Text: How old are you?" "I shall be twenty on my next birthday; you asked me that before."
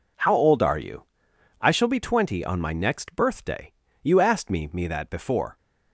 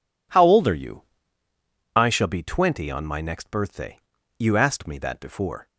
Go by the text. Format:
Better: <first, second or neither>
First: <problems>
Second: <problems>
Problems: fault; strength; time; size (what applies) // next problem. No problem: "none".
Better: second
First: says "me" twice; at 4.7 s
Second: none